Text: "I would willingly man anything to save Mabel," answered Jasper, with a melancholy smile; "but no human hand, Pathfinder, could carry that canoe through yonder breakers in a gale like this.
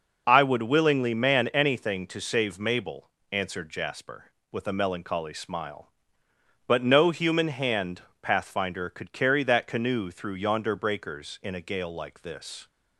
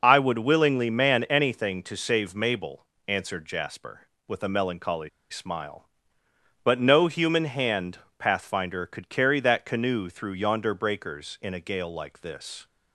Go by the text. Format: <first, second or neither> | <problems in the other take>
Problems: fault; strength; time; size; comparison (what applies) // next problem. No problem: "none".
first | pauses between "melancholy" and "smile"; slight; at 5.0 s; 0.20 s long